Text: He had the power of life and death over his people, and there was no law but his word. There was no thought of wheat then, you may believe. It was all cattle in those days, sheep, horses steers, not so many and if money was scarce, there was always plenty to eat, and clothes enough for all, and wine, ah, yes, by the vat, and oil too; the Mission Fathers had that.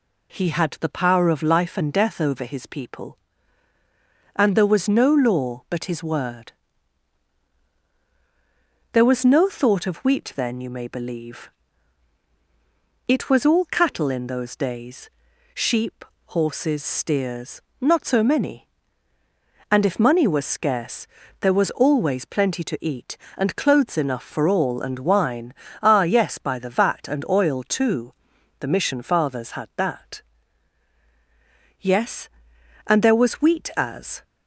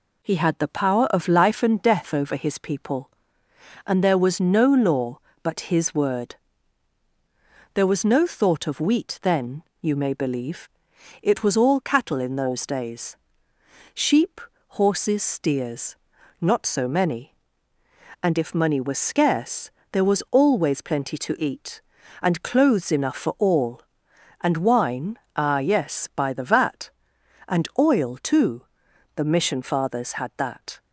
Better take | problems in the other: second | goes on to say "Yes and there was wheat as"; strong; from 31.7 s on; 2.4 s long

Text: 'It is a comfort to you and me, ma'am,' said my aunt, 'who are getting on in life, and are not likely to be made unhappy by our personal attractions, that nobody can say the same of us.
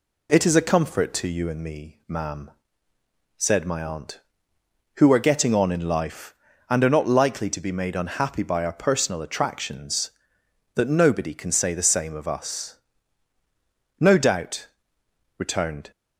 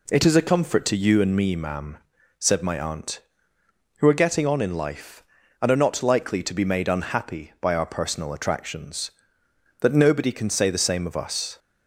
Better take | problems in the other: second | goes on to say "No doubt returned"; strong; from 13.9 s on; 1.9 s long

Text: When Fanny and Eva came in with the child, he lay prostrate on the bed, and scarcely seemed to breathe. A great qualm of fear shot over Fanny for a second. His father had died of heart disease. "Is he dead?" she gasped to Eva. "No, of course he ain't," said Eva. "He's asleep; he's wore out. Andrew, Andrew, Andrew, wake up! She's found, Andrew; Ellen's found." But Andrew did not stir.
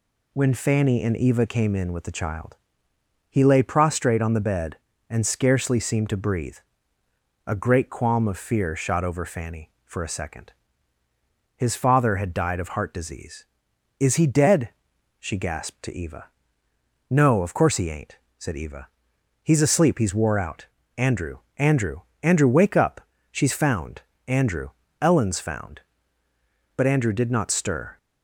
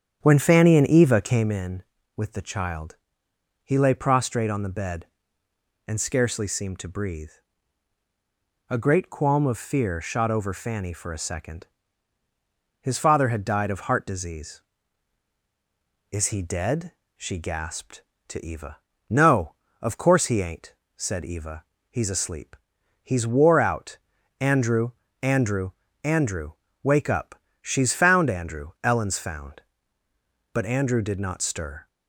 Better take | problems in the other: first | starts louder than the rest; strong; until 1.6 s; 8.5 dB

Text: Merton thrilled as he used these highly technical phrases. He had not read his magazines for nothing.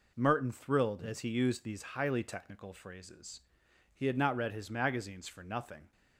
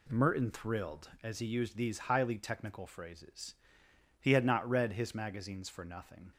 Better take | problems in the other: neither | none

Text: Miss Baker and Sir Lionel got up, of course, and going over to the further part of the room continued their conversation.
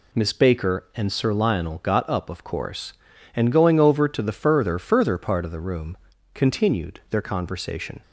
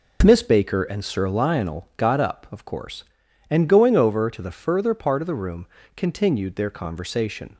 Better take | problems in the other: second | says "further" twice; at 4.7 s // pauses between "room" and "continued"; at 5.9 s; 0.38 s long; slight in the second

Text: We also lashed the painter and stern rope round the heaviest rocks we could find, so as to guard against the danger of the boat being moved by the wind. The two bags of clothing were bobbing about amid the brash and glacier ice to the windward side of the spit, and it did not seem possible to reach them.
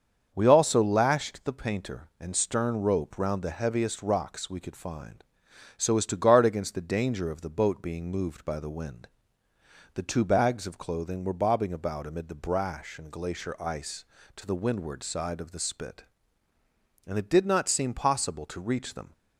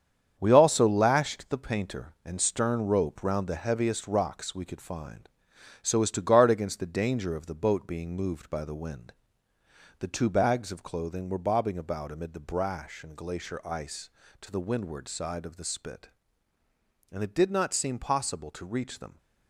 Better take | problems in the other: first | gets quieter; strong; throughout; 7.5 dB // starts louder than the rest; strong; until 1.4 s; 8 dB; also in the first

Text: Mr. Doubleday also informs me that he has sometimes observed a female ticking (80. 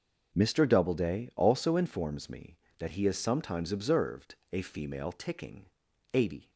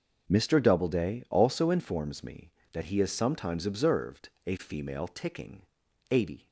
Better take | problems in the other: neither | pauses between "observed" and "a"; slight; the same in both

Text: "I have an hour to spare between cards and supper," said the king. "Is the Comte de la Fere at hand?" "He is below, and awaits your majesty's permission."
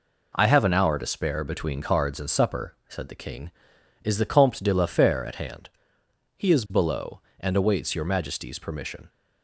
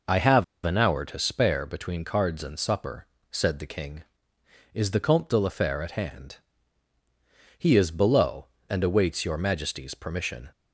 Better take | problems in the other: first | pauses between "have" and "an"; slight; at 0.4 s; 0.21 s long

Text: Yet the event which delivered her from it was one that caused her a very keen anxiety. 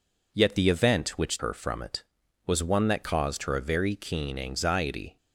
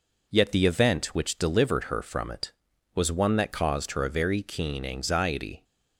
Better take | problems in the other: second | skips "delivered"; at 1.3 s

